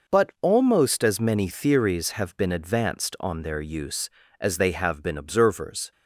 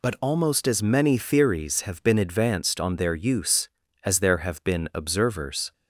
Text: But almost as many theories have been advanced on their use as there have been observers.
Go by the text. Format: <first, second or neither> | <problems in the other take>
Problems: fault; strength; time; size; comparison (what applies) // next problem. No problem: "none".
second | says "they" for "there"; at 4.5 s